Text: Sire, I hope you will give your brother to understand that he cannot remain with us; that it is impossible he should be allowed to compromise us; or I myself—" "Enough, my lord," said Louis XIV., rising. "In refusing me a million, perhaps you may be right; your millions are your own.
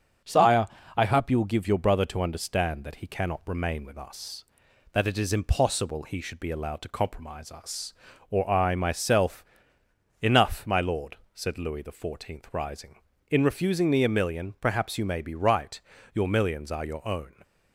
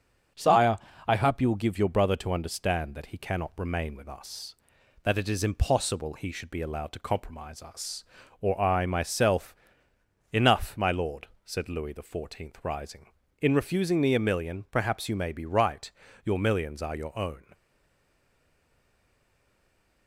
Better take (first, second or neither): first